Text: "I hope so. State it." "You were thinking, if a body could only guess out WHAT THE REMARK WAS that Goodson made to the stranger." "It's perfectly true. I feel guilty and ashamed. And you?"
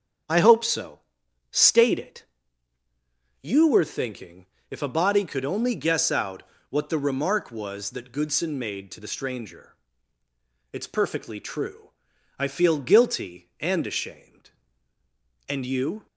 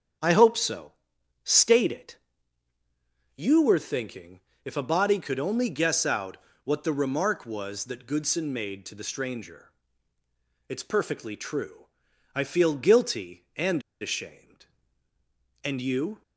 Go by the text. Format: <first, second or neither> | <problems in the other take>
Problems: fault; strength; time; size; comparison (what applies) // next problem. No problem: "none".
first | starts louder than the rest; strong; until 1.7 s; 8 dB; strong in the first // pauses between "out" and "WHAT"; slight; at 6.3 s; 0.26 s long; slight in the first // pauses between "and" and "ashamed"; slight; at 13.8 s; 0.20 s long